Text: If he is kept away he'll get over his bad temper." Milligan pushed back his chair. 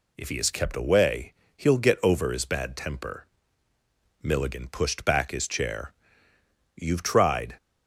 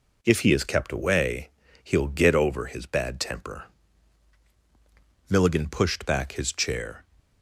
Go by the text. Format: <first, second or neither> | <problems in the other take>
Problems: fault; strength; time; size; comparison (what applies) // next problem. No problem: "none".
second | pauses between "away" and "he'll"; slight; at 1.3 s; 0.24 s long; slight in the second // goes on to say "You've tried"; noticeable; from 6.7 s on; 0.80 s long